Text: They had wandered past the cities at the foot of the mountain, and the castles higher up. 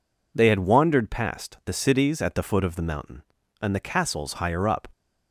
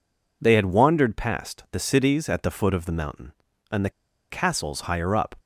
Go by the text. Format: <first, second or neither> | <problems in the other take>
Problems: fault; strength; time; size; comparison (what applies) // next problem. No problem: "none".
first | pauses between "the" and "castles"; at 3.8 s; 0.40 s long